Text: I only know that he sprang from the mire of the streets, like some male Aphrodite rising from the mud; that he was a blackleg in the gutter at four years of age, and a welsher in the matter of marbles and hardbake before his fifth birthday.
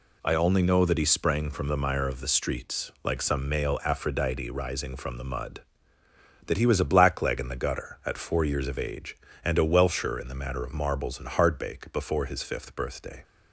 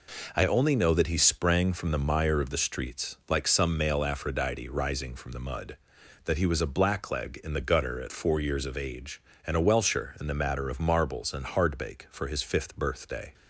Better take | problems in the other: first | says "for" for "before"; at 12.0 s

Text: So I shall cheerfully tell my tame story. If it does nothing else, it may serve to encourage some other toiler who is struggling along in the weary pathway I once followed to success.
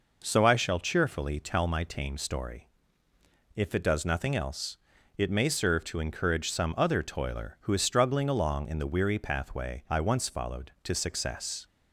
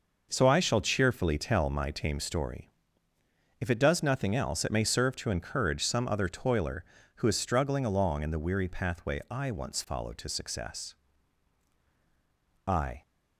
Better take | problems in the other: first | goes on to say "I"; slight; from 12.6 s on; 0.36 s long

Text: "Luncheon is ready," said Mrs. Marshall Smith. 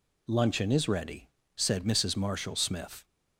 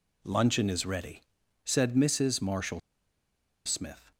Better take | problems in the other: first | pauses between "Marshall" and "Smith"; noticeable; at 2.7 s; 0.86 s long

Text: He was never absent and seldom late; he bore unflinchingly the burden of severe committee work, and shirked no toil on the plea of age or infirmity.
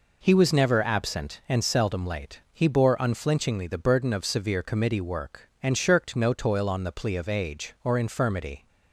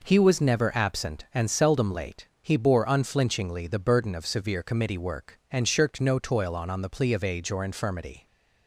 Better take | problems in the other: first | says "on" twice; at 6.7 s

